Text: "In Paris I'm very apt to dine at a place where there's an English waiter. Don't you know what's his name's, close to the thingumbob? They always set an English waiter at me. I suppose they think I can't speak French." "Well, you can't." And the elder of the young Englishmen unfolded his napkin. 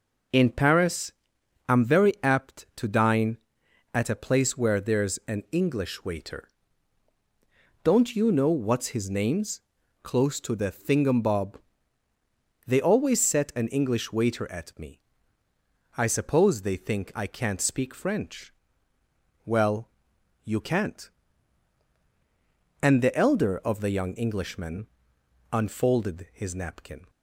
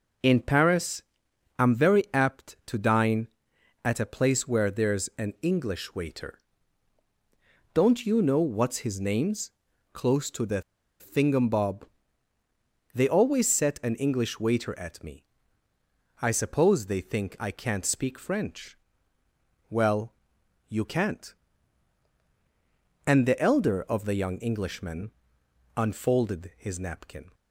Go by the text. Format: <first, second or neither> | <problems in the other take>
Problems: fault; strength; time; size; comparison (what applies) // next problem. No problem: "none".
first | pauses between "Paris" and "I'm"; noticeable; at 1.0 s; 0.56 s long; noticeable in the first // pauses between "the" and "thingumbob"; at 10.6 s; 0.37 s long // pauses between "Englishmen" and "unfolded"; noticeable; at 25.0 s; 0.66 s long; noticeable in the first